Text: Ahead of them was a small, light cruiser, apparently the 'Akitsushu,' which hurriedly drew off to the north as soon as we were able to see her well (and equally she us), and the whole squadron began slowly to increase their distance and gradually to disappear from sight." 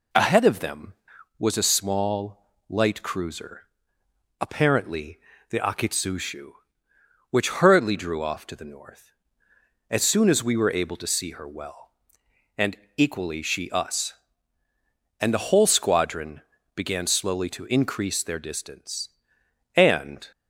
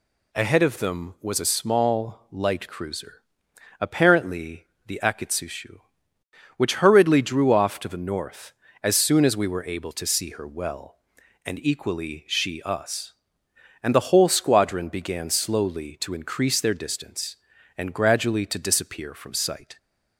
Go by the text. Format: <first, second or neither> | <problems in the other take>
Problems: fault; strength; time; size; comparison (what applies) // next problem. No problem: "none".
second | pauses between "apparently" and "the"; slight; at 5.2 s; 0.30 s long; slight in the second // pauses between "and" and "equally"; slight; at 12.7 s; 0.22 s long // pauses between "squadron" and "began"; slight; at 16.4 s; 0.34 s long // stops before "gradually to disappear from sight"; at 20.3 s